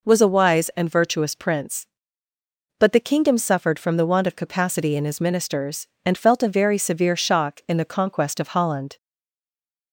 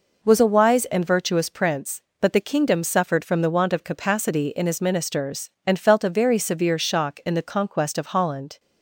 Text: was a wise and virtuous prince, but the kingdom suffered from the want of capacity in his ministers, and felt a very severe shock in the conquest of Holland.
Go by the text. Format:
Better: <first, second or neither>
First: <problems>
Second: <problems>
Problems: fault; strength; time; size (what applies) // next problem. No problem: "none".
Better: second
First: stays silent after the last word; slight; from 8.9 s on; 1.0 s long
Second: none